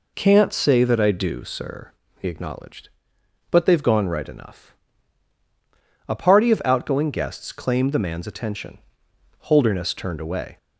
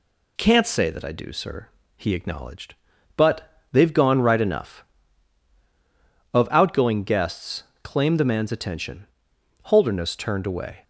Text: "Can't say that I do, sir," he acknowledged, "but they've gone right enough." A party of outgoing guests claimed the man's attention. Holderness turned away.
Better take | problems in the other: first | skips "A party"; at 5.5 s // pauses between "guests" and "claimed"; slight; at 7.6 s; 0.21 s long

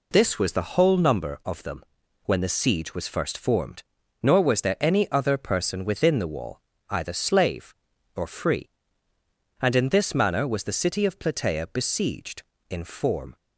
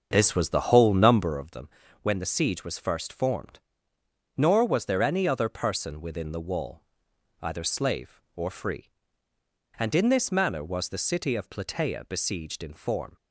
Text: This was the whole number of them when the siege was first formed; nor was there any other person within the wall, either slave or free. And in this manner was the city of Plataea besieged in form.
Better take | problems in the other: first | starts louder than the rest; until 1.5 s; 7 dB // pauses between "them" and "when"; slight; at 1.6 s; 0.34 s long; also in the first

